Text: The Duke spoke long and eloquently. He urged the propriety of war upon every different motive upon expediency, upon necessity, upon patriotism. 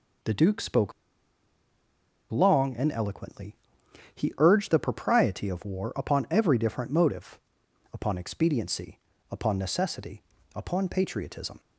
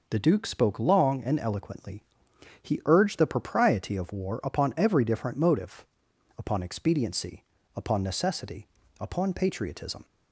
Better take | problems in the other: second | pauses between "spoke" and "long"; strong; at 0.9 s; 1.3 s long // pauses between "motive" and "upon"; noticeable; at 7.3 s; 0.54 s long; noticeable in the second

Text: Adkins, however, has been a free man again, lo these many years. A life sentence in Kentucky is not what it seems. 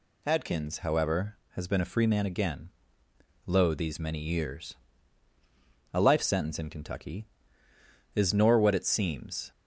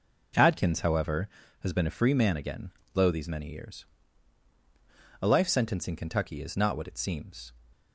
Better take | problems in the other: second | says "nor" for "not"; at 8.3 s

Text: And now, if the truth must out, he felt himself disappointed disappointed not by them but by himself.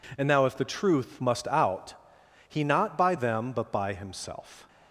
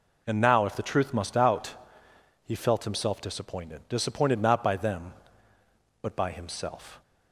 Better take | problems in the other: second | skips "felt himself disappointed disappointed"; at 2.6 s

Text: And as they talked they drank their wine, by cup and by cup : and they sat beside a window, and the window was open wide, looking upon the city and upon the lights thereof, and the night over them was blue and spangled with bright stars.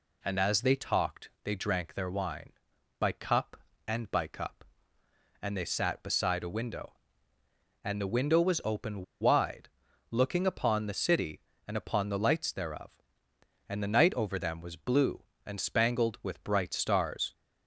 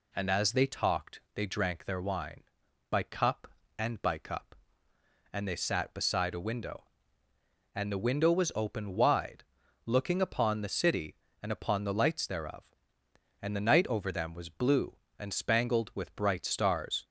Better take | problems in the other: second | pauses between "open" and "wide"; slight; at 9.0 s; 0.17 s long

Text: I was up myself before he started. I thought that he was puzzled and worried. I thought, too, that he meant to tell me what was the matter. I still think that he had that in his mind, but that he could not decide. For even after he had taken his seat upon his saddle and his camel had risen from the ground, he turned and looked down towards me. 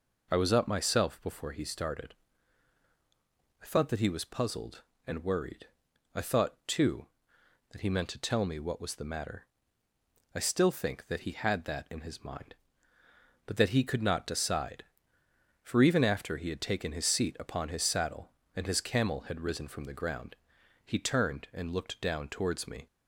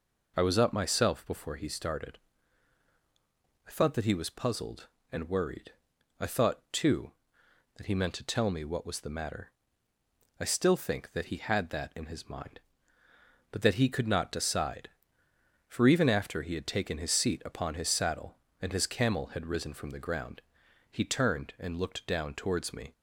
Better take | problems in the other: neither | none

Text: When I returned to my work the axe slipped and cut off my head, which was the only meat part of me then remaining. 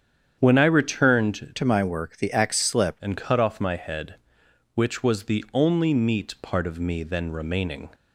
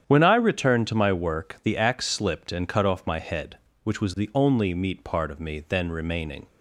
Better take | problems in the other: second | starts louder than the rest; strong; until 1.3 s; 8 dB; strong in the second // changes voice from "to" to "slipped"; from 1.5 to 3.0 s; 1.5 s long

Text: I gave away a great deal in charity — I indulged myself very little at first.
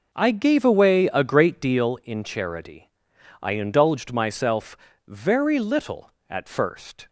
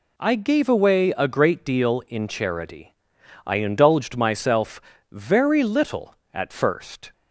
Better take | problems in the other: second | starts louder than the rest; noticeable; until 2.0 s; 5.5 dB // pauses between "myself" and "very"; slight; at 4.7 s; 0.32 s long; slight in the second

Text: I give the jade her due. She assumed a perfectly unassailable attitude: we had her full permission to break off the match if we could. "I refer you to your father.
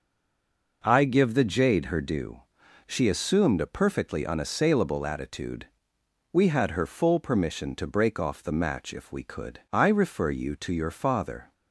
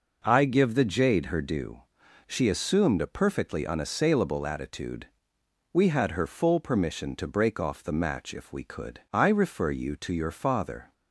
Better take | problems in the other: second | stays silent before the first word; slight; until 0.8 s; 0.8 s long

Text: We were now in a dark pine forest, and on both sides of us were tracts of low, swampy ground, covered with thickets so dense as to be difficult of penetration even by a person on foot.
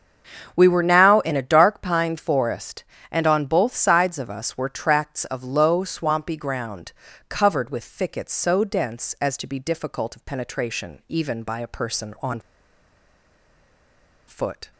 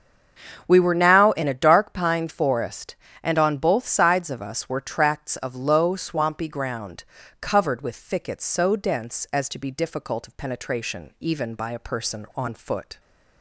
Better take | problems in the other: second | starts louder than the rest; strong; until 1.5 s; 7 dB; strong in the second // pauses between "on" and "foot"; strong; at 12.3 s; 1.8 s long

